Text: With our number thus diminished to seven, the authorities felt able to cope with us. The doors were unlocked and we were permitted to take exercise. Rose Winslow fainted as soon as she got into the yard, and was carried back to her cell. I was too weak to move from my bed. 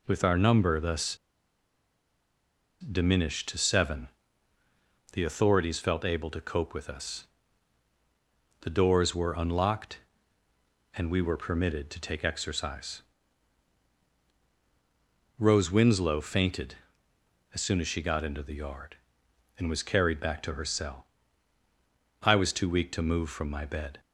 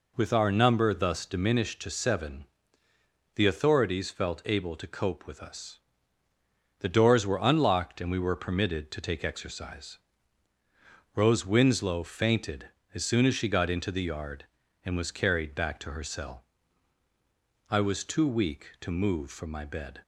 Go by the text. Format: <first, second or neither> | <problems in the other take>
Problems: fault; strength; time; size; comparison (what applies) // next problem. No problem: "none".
second | pauses between "thus" and "diminished"; strong; at 1.1 s; 1.6 s long